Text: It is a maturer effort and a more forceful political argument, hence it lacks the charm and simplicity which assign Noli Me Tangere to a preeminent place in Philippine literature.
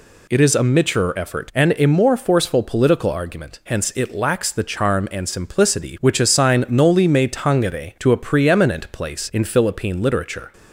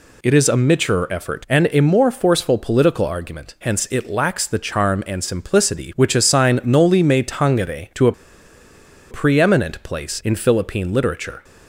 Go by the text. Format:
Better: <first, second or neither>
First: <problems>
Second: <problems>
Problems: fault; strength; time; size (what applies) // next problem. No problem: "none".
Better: first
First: none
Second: pauses between "a" and "preeminent"; at 8.1 s; 0.98 s long